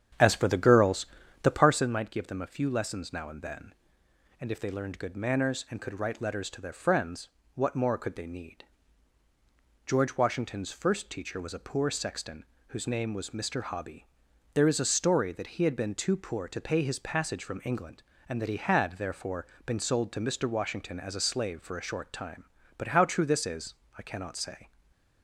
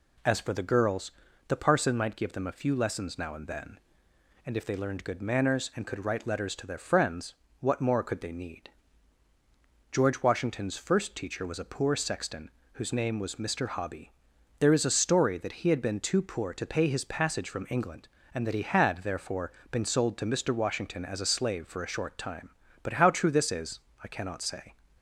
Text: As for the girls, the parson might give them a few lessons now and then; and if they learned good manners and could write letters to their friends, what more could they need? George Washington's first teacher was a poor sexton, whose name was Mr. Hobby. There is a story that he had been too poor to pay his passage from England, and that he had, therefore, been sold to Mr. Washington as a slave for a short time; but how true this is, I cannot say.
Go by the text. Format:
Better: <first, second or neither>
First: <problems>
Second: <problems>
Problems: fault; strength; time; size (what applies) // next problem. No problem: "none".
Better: second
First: starts louder than the rest; strong; until 1.9 s; 9 dB // stays silent after the last word; slight; from 24.6 s on; 0.6 s long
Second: none